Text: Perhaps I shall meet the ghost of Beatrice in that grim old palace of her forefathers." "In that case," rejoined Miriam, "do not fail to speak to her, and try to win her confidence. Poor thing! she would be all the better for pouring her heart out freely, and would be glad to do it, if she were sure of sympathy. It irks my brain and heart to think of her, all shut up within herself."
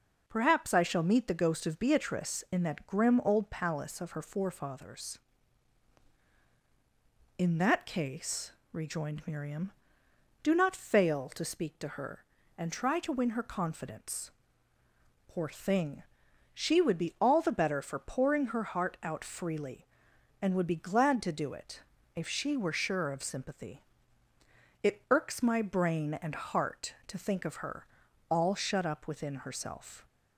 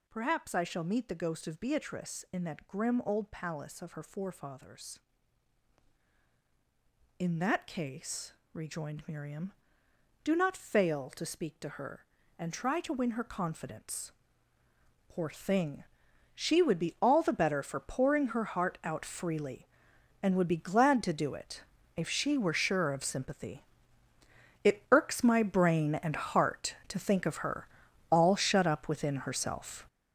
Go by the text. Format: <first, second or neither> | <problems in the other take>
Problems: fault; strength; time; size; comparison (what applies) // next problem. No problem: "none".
first | gets louder; strong; throughout; 9 dB